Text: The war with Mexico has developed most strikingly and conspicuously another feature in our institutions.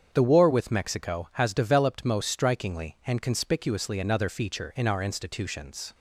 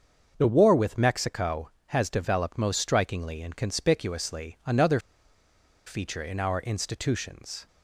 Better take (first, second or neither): first